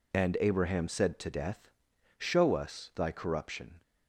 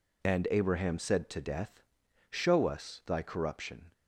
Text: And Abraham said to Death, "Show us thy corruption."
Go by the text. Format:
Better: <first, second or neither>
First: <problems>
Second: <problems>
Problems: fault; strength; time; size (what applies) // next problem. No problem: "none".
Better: neither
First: none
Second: none